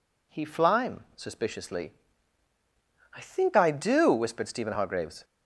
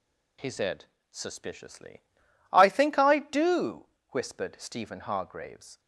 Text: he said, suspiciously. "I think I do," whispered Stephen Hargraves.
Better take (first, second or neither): second